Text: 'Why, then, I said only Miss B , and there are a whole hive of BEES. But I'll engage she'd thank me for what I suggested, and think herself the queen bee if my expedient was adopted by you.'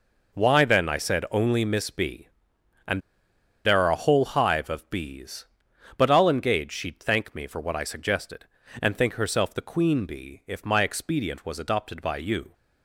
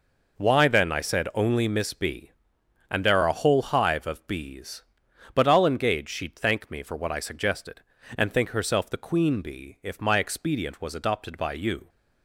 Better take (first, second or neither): second